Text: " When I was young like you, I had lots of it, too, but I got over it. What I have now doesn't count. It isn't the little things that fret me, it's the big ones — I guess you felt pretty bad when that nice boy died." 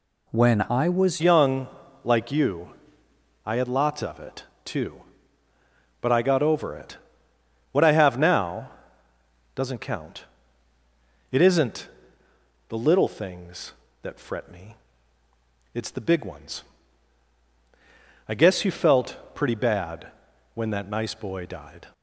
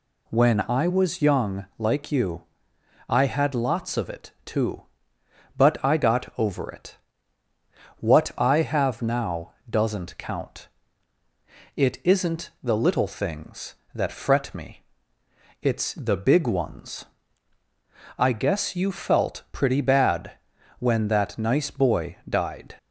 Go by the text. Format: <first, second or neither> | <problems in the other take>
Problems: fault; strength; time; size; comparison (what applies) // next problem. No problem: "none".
second | changes voice at "young"; from 1.2 s on; 20.7 s long // pauses between "young" and "like"; slight; at 1.6 s; 0.34 s long // pauses between "now" and "doesn't"; noticeable; at 8.7 s; 0.84 s long; slight in the second // pauses between "isn't" and "the"; noticeable; at 11.8 s; 0.80 s long // pauses between "felt" and "pretty"; slight; at 19.1 s; 0.18 s long // pauses between "bad" and "when"; at 20.1 s; 0.44 s long; also in the second